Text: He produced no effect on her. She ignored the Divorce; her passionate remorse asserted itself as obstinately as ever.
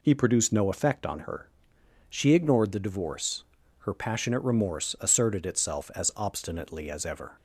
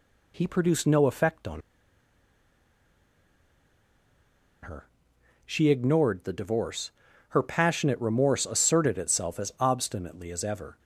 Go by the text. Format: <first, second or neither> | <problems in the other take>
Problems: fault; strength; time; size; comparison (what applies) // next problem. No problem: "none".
first | pauses between "on" and "her"; strong; at 1.6 s; 3.0 s long